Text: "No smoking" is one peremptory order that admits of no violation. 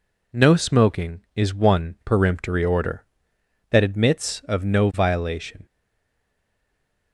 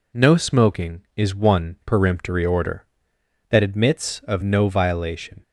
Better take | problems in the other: second | stays silent after the last word; noticeable; from 5.6 s on; 1.5 s long

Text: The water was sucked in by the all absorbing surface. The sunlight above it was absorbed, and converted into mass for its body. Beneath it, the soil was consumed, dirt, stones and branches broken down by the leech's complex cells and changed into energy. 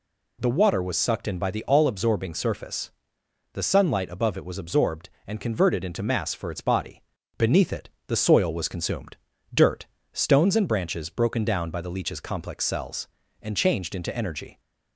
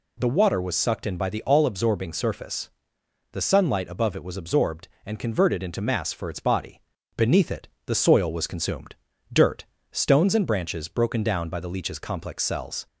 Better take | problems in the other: first | stops before "and changed into energy"; at 12.8 s

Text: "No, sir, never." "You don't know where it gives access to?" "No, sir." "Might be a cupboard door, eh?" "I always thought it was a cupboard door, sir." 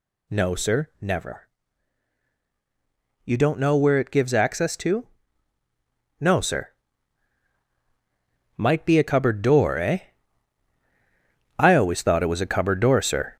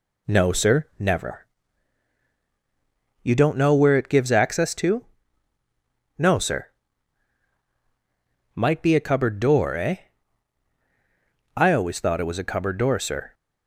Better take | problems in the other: second | gets louder; throughout; 6.5 dB

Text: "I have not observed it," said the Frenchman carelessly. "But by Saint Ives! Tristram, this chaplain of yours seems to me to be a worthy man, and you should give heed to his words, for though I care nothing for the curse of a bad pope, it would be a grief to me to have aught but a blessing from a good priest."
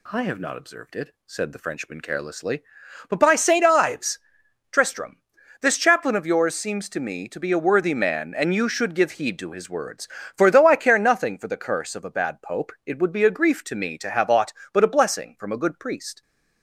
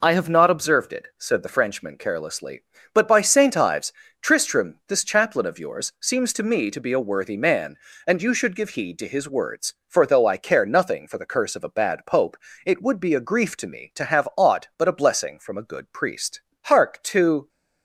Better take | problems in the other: first | goes on to say "Hark to"; noticeable; from 16.6 s on; 0.82 s long

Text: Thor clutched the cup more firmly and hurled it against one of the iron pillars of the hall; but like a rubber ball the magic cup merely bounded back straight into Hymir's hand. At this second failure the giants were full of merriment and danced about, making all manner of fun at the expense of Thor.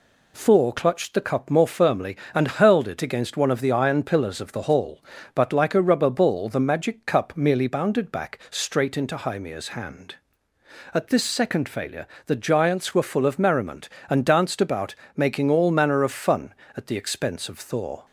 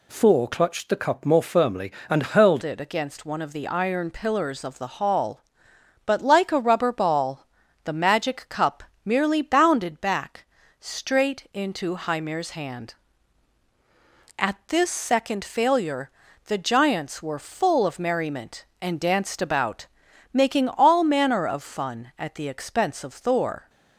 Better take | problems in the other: first | changes voice at "it"; from 2.6 s on; 21.0 s long // pauses between "ball" and "the"; at 7.4 s; 0.38 s long // pauses between "cup" and "merely"; slight; at 8.8 s; 0.22 s long // pauses between "back" and "straight"; slight; at 10.4 s; 0.34 s long // pauses between "failure" and "the"; slight; at 16.0 s; 0.36 s long; slight in the first

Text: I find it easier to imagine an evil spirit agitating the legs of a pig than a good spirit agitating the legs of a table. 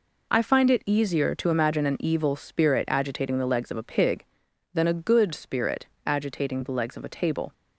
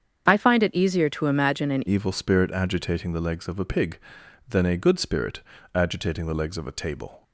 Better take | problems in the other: first | starts louder than the rest; strong; until 1.3 s; 7 dB // changes voice at "evil"; from 1.8 s on; 5.4 s long // pauses between "spirit" and "agitating"; slight; at 5.4 s; 0.34 s long; slight in the first

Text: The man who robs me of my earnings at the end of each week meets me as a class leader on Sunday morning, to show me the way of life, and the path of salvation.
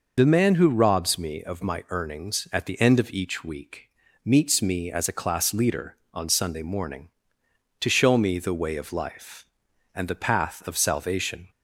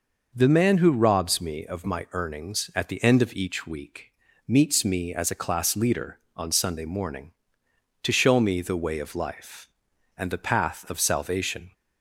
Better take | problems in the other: second | loses the start of "The"; at 0.1 s; 55 ms // pauses between "week" and "meets"; slight; at 3.9 s; 0.34 s long; slight in the second

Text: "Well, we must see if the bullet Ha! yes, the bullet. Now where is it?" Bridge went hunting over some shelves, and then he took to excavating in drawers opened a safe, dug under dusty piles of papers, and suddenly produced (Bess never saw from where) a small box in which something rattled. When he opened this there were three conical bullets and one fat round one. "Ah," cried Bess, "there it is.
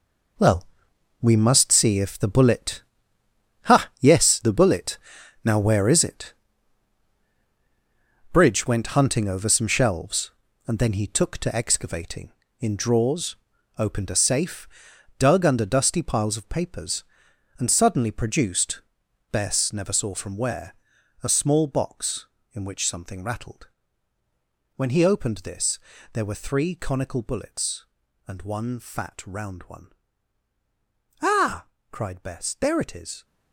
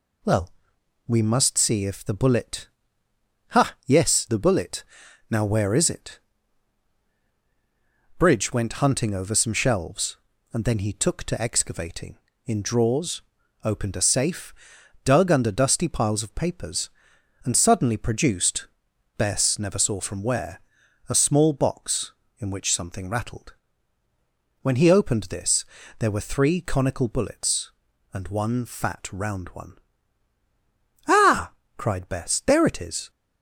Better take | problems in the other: second | gets quieter; strong; throughout; 10 dB // pauses between "bullet" and "Ha"; noticeable; at 2.8 s; 0.86 s long; noticeable in the second // pauses between "drawers" and "opened"; at 13.3 s; 0.40 s long; also in the second // pauses between "this" and "there"; slight; at 25.7 s; 0.32 s long; slight in the second

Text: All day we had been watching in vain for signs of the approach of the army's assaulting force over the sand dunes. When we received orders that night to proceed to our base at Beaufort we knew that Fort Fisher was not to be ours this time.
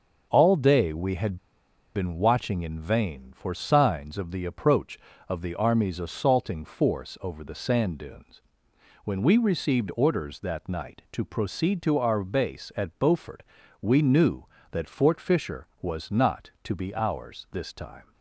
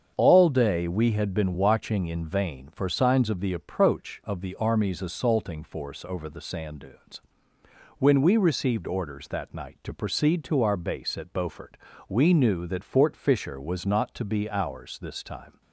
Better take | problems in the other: second | starts louder than the rest; until 1.3 s; 6.5 dB; strong in the second // pauses between "had" and "been"; noticeable; at 1.3 s; 0.58 s long // pauses between "Beaufort" and "we"; at 13.4 s; 0.38 s long; slight in the second

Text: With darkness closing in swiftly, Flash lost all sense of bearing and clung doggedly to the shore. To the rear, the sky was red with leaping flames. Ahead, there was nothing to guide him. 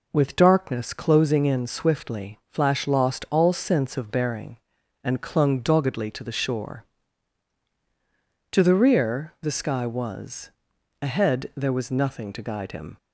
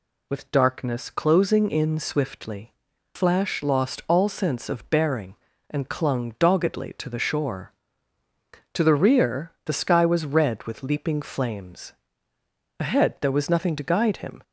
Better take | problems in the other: second | skips "red with leaping flames"; at 10.7 s

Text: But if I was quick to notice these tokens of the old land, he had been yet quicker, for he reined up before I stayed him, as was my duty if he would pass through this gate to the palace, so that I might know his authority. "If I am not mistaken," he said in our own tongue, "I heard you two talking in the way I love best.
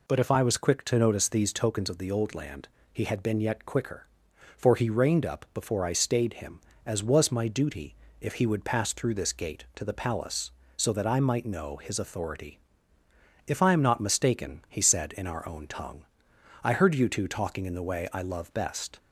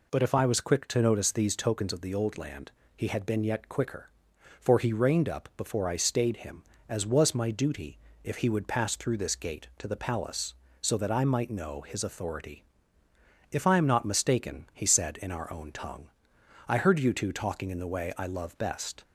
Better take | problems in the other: neither | pauses between "duty" and "if"; slight; the same in both

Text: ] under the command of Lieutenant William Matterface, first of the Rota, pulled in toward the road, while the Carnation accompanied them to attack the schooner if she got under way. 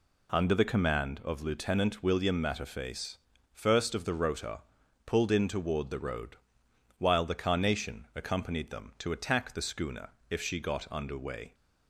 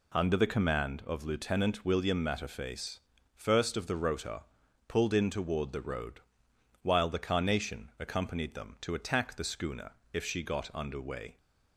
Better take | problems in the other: neither | pauses between "schooner" and "if"; slight; the same in both

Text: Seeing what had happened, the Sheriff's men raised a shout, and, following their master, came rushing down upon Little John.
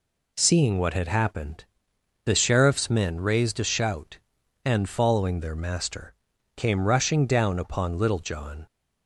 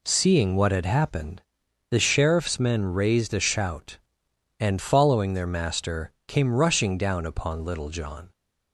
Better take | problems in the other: neither | none

